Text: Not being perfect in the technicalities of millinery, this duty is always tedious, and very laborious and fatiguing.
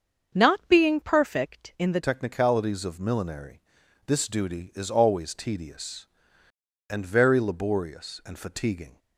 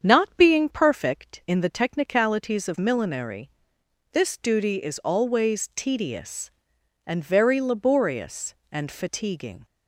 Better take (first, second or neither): second